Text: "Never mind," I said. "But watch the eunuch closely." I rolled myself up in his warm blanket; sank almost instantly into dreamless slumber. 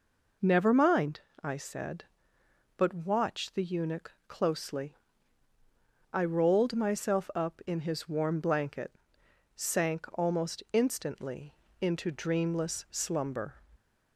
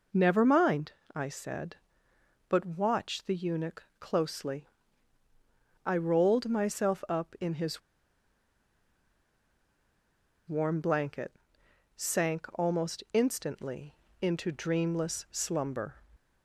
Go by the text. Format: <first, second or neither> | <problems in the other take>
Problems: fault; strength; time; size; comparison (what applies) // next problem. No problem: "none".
first | pauses between "eunuch" and "closely"; slight; at 3.8 s; 0.16 s long; slight in the first // pauses between "his" and "warm"; strong; at 7.8 s; 2.6 s long // pauses between "instantly" and "into"; slight; at 13.9 s; 0.26 s long; slight in the first